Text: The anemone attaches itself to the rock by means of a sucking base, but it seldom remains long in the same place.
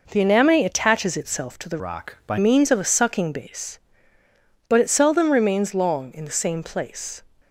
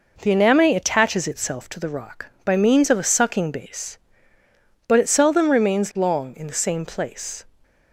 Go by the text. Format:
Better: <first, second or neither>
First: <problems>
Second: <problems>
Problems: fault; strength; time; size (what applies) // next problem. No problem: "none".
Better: second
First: changes voice from "rock" to "by"; from 1.7 to 2.3 s; 0.6 s long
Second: none